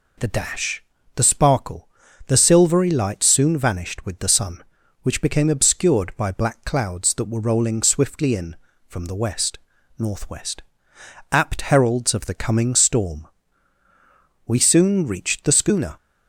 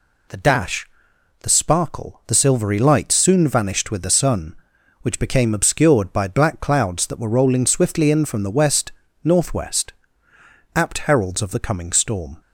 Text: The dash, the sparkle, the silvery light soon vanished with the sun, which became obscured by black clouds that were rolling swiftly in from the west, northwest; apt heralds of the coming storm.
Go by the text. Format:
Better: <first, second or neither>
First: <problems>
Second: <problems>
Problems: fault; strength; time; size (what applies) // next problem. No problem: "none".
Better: second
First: goes on to say "We soon reached the schooner"; from 14.4 s on; 1.5 s long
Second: none